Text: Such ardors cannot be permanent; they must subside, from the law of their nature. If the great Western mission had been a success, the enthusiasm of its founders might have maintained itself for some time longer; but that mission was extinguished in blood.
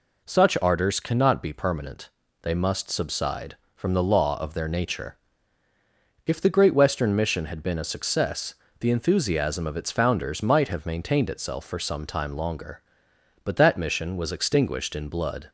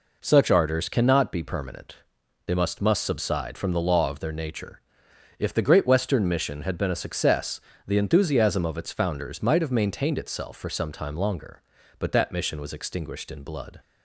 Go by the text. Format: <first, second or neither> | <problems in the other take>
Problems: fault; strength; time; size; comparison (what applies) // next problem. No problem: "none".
first | says "must" twice; at 2.8 s